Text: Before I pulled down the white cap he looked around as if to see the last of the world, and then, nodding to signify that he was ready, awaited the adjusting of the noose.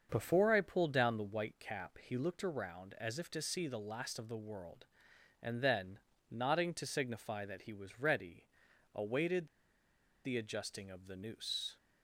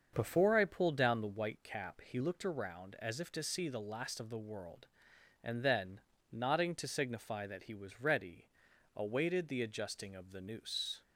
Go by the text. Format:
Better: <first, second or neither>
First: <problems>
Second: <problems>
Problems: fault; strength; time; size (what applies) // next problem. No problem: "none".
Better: second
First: starts louder than the rest; until 1.1 s; 6.5 dB // pauses between "awaited" and "the"; noticeable; at 9.4 s; 0.78 s long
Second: starts louder than the rest; until 1.1 s; 6.5 dB